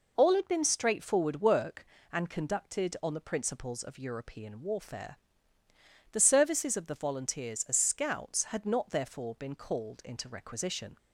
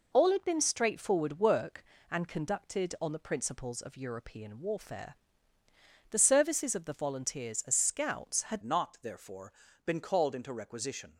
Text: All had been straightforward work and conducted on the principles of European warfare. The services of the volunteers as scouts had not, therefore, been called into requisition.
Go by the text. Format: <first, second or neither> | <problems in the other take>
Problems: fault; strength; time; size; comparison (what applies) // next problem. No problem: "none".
first | changes voice at "not"; from 8.6 s on; 2.5 s long